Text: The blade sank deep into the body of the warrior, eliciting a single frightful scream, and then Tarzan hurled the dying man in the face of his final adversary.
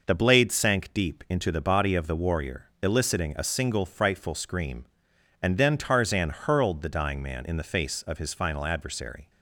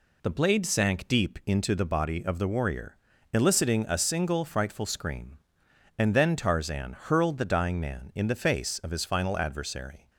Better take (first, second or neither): neither